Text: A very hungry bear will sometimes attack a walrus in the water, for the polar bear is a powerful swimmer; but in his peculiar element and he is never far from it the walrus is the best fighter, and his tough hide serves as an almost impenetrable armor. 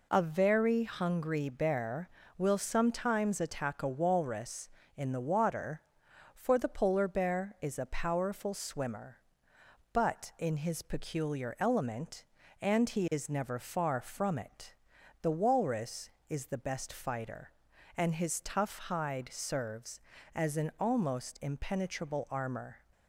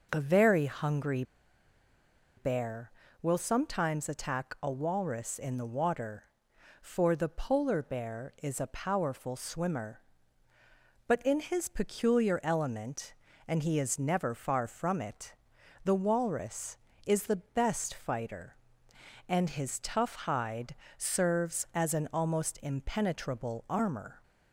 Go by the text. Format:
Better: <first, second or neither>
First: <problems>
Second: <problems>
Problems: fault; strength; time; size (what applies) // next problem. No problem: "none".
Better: first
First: pauses between "it" and "the"; noticeable; at 14.7 s; 0.48 s long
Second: pauses between "hungry" and "bear"; at 1.2 s; 1.1 s long // pauses between "it" and "the"; noticeable; at 15.3 s; 0.50 s long // pauses between "hide" and "serves"; slight; at 20.7 s; 0.22 s long